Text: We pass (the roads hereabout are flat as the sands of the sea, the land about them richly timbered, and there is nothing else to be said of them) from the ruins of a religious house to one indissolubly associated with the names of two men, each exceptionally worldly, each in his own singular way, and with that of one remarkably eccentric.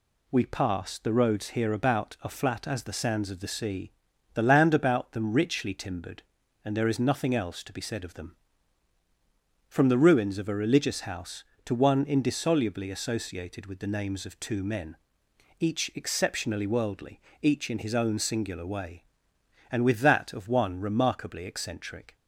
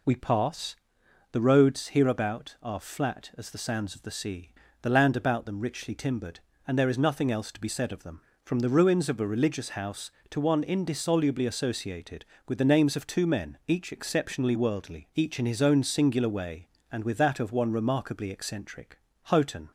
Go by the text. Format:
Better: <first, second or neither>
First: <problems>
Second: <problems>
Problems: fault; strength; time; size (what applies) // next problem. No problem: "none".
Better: first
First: none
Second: goes on to say "Houghton"; slight; from 19.2 s on; 0.48 s long